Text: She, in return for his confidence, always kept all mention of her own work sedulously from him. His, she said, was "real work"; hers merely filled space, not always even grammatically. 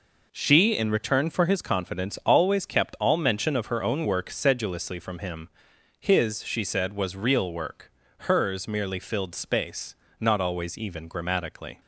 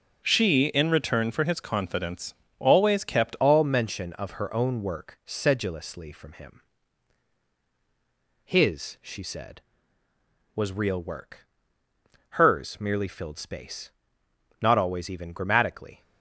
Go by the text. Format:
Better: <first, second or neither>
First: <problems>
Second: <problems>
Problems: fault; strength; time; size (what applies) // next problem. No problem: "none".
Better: first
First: none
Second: starts louder than the rest; until 1.2 s; 7 dB // changes voice at "all"; from 3.3 s on; 12.7 s long